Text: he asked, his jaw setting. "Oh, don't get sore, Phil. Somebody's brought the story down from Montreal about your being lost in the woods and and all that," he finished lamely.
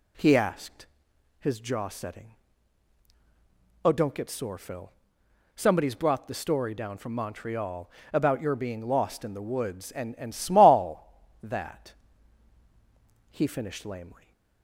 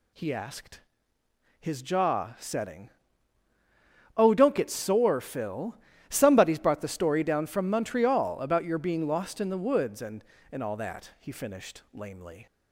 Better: second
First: pauses between "Montreal" and "about"; slight; at 7.8 s; 0.22 s long // says "small" for "all"; at 10.3 s // stays silent after the last word; slight; from 14.1 s on; 0.5 s long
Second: none

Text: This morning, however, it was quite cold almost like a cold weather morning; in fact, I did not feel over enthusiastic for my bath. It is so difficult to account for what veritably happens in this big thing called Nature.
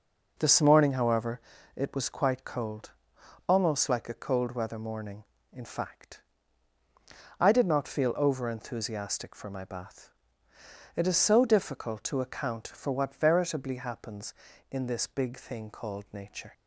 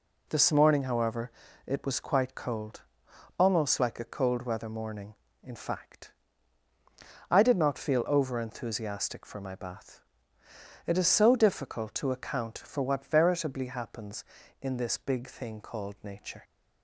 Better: second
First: starts louder than the rest; noticeable; until 1.3 s; 5 dB // pauses between "cold" and "almost"; noticeable; at 2.9 s; 0.58 s long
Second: pauses between "cold" and "almost"; noticeable; at 2.8 s; 0.58 s long

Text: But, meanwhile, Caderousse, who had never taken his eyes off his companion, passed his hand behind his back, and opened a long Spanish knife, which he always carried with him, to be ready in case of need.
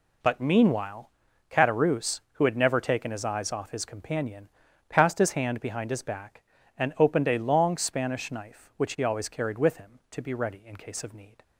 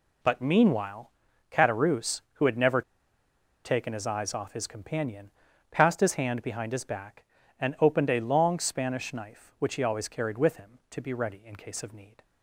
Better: first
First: none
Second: pauses between "never" and "taken"; noticeable; at 2.8 s; 0.83 s long

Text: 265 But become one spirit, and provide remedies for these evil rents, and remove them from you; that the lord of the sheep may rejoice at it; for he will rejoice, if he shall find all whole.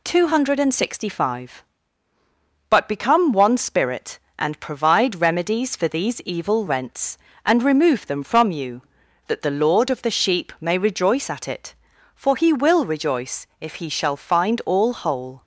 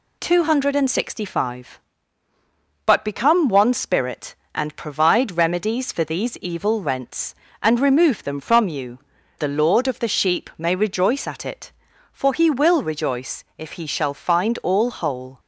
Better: first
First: none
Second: skips "that"; at 9.1 s

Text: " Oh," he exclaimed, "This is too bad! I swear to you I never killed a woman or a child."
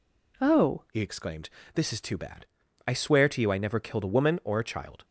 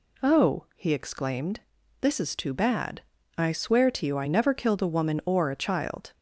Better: second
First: changes voice at "he"; from 0.9 s on; 4.1 s long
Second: none

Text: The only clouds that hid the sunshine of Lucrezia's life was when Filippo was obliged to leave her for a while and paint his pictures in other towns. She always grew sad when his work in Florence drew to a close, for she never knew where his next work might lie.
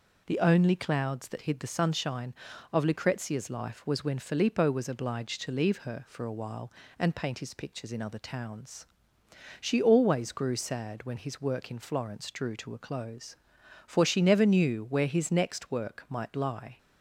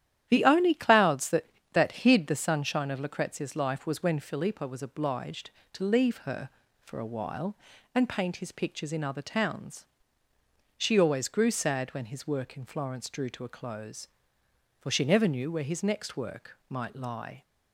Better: first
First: none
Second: starts louder than the rest; strong; until 1.3 s; 11 dB // says "that" twice; at 1.7 s

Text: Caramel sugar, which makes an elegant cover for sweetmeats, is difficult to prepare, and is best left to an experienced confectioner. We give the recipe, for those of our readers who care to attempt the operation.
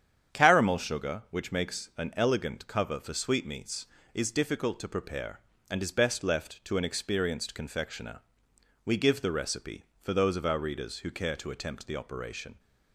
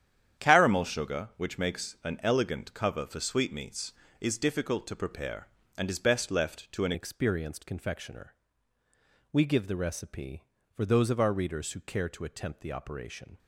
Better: first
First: starts louder than the rest; strong; until 1.4 s; 8.5 dB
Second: starts louder than the rest; strong; until 1.4 s; 9.5 dB // changes voice at "experienced"; from 6.9 s on; 6.4 s long

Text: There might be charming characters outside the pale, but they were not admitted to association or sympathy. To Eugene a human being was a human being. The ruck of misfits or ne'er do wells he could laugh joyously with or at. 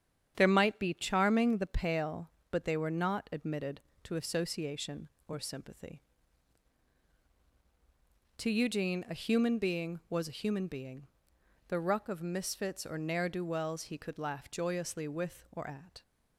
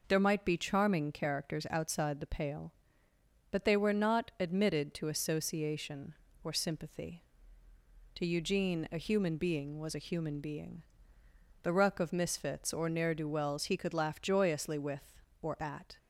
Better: second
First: starts louder than the rest; strong; until 1.3 s; 8.5 dB // skips "characters outside"; at 1.5 s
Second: none

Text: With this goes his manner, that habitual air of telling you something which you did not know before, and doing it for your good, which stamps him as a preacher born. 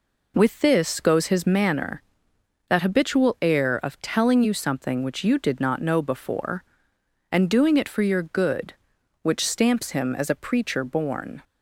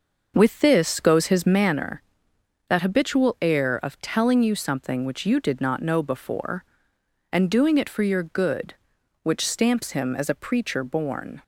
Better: first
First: none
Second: starts louder than the rest; noticeable; until 1.8 s; 6 dB

